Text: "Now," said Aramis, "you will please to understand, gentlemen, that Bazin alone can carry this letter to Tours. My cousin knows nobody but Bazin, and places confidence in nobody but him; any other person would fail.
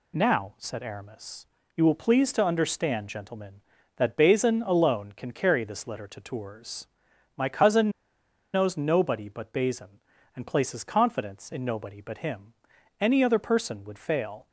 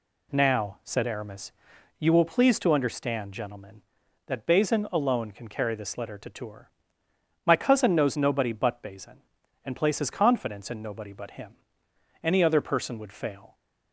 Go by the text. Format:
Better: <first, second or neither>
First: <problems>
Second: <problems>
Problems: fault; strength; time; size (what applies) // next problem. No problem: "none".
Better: second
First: pauses between "cousin" and "knows"; noticeable; at 7.9 s; 0.63 s long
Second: none